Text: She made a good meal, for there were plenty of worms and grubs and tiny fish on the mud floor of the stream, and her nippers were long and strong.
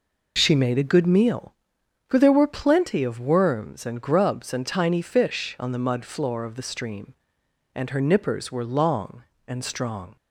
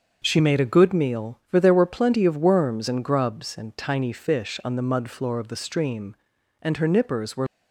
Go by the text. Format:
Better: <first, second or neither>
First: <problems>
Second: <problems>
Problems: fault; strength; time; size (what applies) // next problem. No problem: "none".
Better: first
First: none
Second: starts louder than the rest; until 1.2 s; 6.5 dB // stops before "long and strong"; at 7.4 s